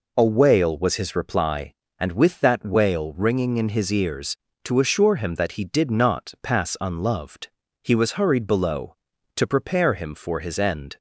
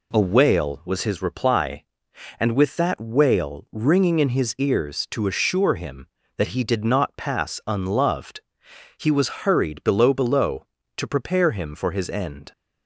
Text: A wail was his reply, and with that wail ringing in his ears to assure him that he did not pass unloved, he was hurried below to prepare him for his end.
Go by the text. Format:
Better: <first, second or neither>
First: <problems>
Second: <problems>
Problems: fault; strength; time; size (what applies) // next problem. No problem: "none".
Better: first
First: none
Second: says "below" twice; at 10.1 s